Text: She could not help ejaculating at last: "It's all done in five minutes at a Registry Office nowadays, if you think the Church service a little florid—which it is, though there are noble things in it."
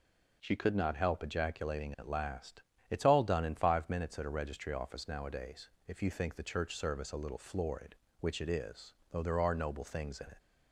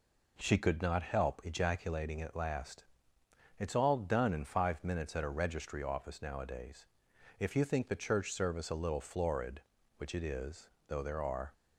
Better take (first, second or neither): first